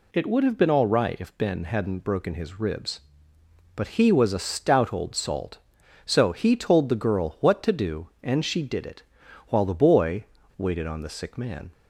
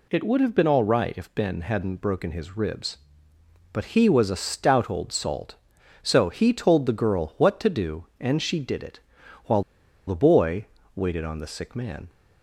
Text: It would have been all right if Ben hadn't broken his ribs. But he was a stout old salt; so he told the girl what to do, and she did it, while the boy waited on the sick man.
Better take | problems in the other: first | pauses between "while" and "the"; at 9.6 s; 0.45 s long // pauses between "boy" and "waited"; slight; at 10.6 s; 0.28 s long; slight in the first

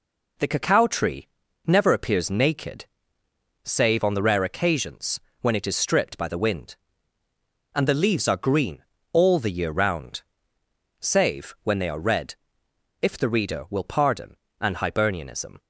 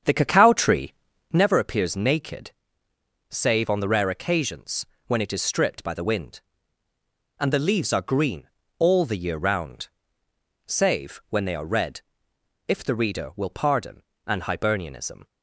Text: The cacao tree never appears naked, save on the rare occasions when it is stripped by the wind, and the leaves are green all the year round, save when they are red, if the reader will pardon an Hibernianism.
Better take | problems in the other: first | starts louder than the rest; strong; until 1.4 s; 8 dB // pauses between "tree" and "never"; slight; at 0.9 s; 0.36 s long; slight in the first // pauses between "occasions" and "when"; slight; at 4.8 s; 0.20 s long; slight in the first // pauses between "green" and "all"; slight; at 8.4 s; 0.30 s long; slight in the first // pauses between "pardon" and "an"; slight; at 14.0 s; 0.24 s long; slight in the first

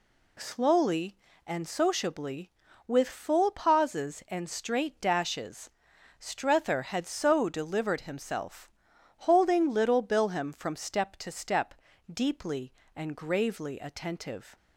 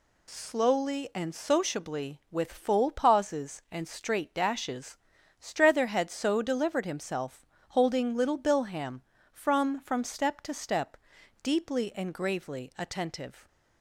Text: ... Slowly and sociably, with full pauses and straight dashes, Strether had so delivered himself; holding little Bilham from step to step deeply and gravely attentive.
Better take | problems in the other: first | says "from" twice; at 9.7 s // pauses between "step" and "deeply"; at 10.9 s; 0.42 s long; also in the first

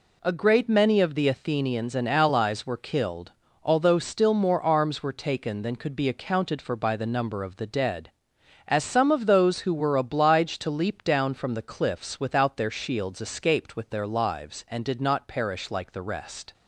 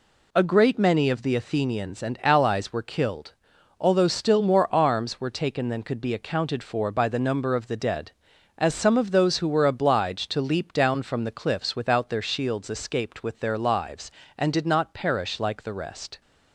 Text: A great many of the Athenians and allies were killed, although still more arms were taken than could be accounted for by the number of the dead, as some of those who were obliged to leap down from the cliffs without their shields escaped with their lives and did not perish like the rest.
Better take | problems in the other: neither | none

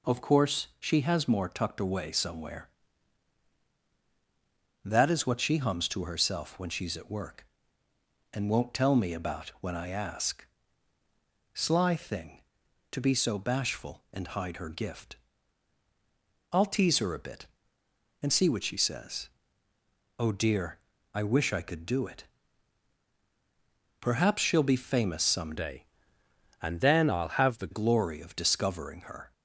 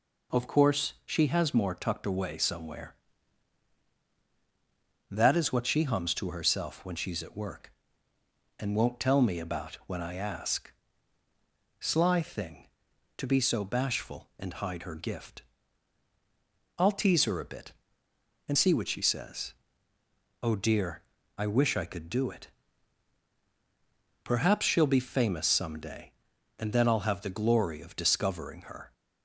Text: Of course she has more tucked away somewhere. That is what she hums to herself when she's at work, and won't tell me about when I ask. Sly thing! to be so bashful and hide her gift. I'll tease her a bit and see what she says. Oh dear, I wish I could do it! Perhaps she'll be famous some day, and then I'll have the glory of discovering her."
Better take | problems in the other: second | changes voice from "day" to "the"; from 25.5 to 27.7 s; 2.2 s long

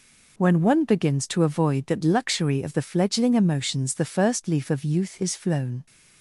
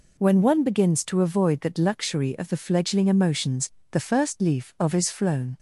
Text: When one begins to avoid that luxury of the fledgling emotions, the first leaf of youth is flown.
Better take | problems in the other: first | skips "youth"; at 4.9 s

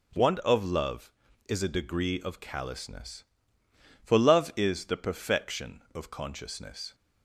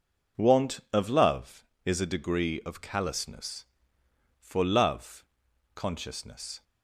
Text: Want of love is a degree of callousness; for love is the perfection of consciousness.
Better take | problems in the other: first | skips "is the perfection of"; at 5.4 s

